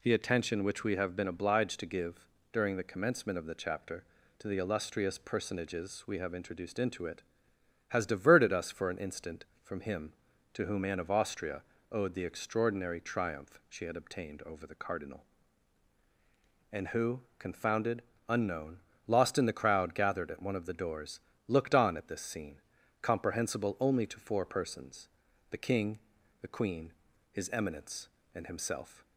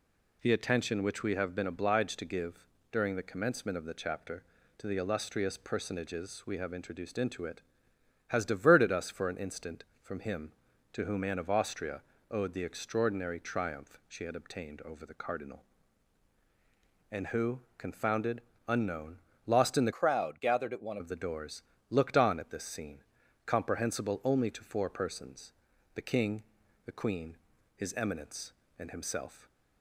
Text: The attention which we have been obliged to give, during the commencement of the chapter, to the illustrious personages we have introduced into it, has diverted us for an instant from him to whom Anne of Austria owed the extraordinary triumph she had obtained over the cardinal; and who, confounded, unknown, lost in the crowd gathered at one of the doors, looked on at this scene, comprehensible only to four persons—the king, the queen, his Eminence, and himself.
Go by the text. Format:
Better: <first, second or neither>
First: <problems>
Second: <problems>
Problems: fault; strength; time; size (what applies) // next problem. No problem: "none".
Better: first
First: pauses between "Austria" and "owed"; slight; at 11.6 s; 0.30 s long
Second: pauses between "Austria" and "owed"; slight; at 12.0 s; 0.30 s long // changes voice from "crowd" to "one"; from 19.9 to 20.9 s; 1.0 s long